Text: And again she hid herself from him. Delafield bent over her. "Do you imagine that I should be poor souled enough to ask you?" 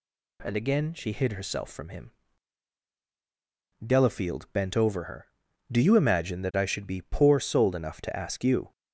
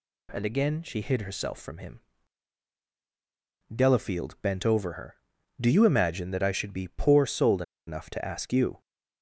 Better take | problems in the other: first | pauses between "souled" and "enough"; slight; at 7.6 s; 0.25 s long

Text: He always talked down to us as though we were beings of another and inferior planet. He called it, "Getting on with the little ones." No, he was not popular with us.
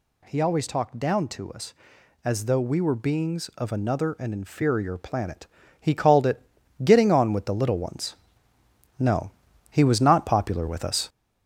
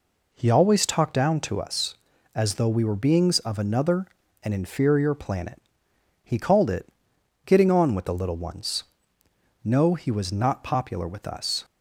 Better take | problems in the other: second | gets louder; throughout; 4 dB

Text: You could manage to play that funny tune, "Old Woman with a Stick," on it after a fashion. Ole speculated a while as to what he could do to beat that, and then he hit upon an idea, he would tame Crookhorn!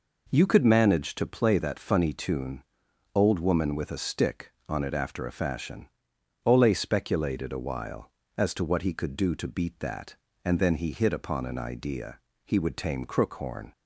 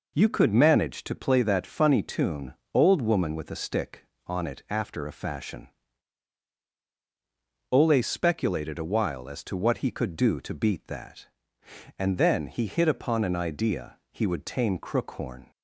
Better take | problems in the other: neither | none

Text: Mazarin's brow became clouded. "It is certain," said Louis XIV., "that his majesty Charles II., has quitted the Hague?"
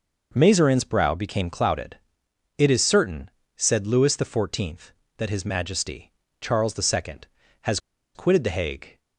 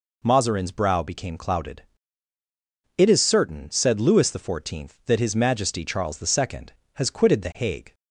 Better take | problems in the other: second | pauses between "majesty" and "Charles"; slight; at 6.1 s; 0.30 s long // pauses between "has" and "quitted"; at 7.7 s; 0.36 s long

